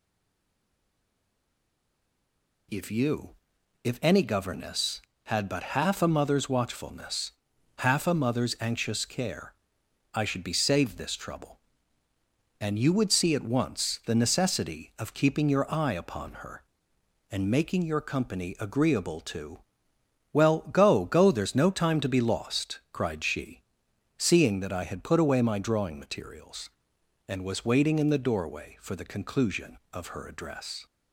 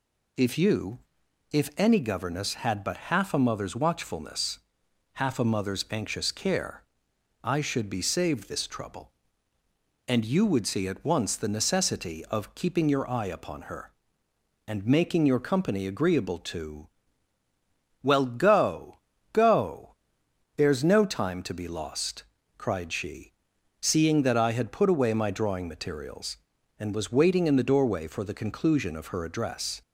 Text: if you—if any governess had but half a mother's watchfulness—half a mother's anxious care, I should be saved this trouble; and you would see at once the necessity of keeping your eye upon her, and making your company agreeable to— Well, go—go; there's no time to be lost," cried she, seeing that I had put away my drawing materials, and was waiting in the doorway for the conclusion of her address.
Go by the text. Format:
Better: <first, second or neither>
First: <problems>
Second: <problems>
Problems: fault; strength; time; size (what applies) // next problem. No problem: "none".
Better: second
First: stays silent before the first word; strong; until 2.6 s; 2.6 s long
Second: none